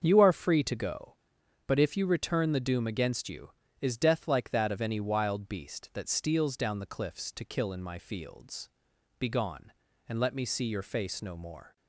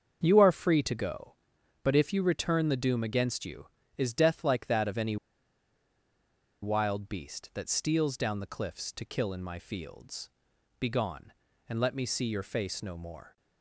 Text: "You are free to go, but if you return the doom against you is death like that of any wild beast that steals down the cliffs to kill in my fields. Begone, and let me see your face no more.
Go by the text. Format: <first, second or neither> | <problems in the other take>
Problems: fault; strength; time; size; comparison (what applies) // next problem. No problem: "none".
first | starts louder than the rest; until 1.2 s; 7 dB; also in the first // pauses between "any" and "wild"; strong; at 5.1 s; 1.4 s long